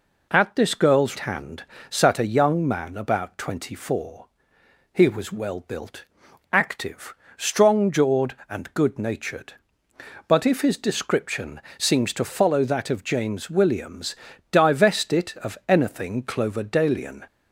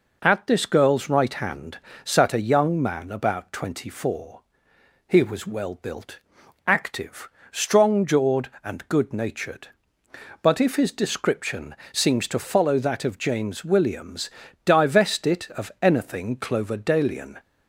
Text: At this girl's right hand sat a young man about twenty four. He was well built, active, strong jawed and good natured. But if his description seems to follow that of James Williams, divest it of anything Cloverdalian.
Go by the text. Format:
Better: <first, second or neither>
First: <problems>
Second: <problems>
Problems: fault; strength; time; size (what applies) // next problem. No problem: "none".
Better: second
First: skips "right"; at 1.1 s // pauses between "hand" and "sat"; slight; at 1.6 s; 0.26 s long // pauses between "description" and "seems"; slight; at 11.6 s; 0.16 s long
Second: pauses between "hand" and "sat"; slight; at 1.7 s; 0.26 s long // pauses between "description" and "seems"; slight; at 11.7 s; 0.16 s long